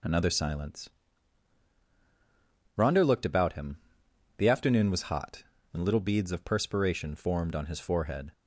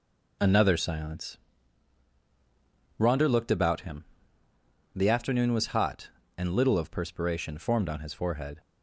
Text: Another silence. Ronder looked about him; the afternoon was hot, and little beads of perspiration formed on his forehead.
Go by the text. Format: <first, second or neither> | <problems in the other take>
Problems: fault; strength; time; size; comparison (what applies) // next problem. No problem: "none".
first | skips "beads"; at 6.7 s